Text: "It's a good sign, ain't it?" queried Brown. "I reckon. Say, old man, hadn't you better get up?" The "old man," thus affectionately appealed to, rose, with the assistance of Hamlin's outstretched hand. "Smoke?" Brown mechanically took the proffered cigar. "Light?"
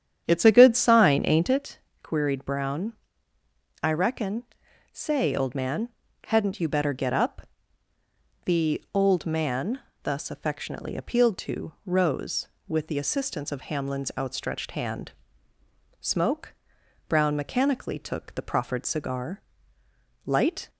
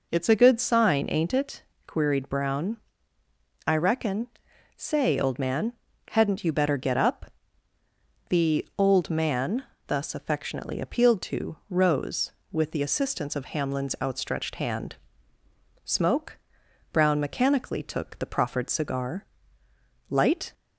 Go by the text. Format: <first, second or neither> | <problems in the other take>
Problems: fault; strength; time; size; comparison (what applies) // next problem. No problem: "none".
second | starts louder than the rest; strong; until 1.6 s; 9 dB